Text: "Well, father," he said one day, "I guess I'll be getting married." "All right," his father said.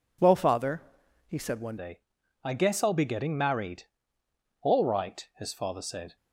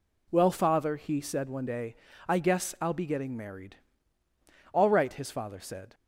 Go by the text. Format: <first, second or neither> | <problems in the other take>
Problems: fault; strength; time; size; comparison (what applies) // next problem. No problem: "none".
second | changes voice at "day"; from 1.7 s on; 4.4 s long